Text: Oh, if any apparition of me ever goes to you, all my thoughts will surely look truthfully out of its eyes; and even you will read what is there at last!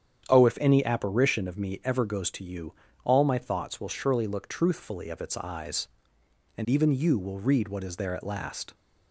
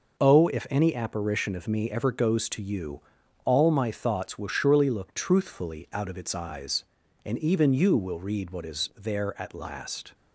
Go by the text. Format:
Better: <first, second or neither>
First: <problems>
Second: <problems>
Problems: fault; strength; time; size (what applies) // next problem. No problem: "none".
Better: second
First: starts louder than the rest; strong; until 1.3 s; 9 dB // skips "out"; at 5.1 s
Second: none